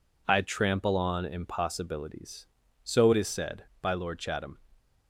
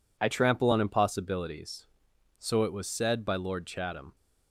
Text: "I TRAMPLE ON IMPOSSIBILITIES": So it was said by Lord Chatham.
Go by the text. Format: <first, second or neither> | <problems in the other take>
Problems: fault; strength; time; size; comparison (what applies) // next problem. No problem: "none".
second | says "is" for "was"; at 3.1 s